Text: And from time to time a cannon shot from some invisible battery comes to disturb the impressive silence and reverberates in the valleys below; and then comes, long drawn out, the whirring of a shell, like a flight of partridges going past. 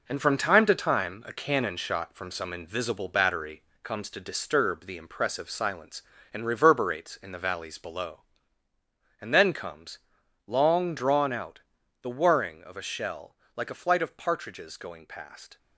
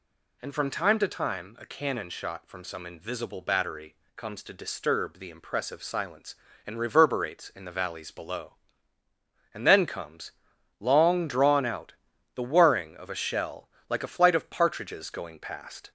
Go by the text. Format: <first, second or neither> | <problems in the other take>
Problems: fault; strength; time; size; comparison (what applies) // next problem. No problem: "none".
second | gets quieter; strong; throughout; 7 dB // pauses between "battery" and "comes"; slight; at 3.6 s; 0.20 s long; slight in the second